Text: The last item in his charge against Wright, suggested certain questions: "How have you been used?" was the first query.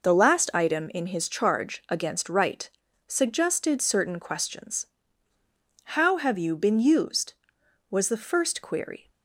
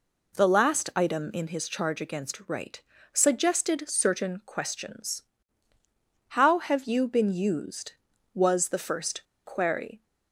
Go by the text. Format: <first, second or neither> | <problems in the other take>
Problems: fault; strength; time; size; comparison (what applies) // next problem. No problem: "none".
first | pauses between "first" and "query"; slight; at 9.2 s; 0.22 s long